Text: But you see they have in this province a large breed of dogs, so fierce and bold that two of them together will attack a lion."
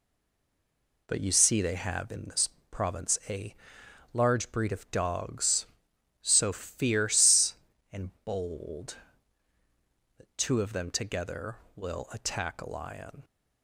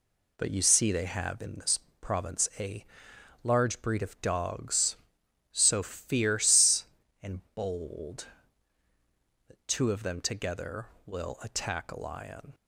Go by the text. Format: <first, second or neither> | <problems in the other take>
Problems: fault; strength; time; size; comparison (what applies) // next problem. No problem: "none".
second | stays silent before the first word; until 1.0 s; 1.0 s long // pauses between "this" and "province"; slight; at 2.4 s; 0.22 s long; slight in the second // pauses between "a" and "large"; noticeable; at 3.5 s; 0.58 s long; noticeable in the second